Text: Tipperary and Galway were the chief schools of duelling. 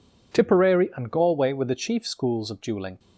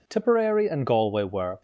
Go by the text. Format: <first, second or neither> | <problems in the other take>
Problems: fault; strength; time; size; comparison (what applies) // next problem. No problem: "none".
first | stops before "the chief schools of duelling"; at 1.5 s